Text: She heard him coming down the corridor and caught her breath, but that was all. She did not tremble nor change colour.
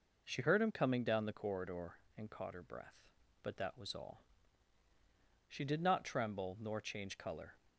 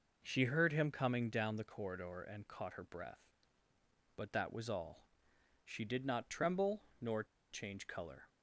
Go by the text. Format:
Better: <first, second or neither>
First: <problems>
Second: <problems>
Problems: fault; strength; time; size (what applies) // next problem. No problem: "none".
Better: first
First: none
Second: pauses between "tremble" and "nor"; slight; at 6.8 s; 0.16 s long // pauses between "nor" and "change"; slight; at 7.2 s; 0.27 s long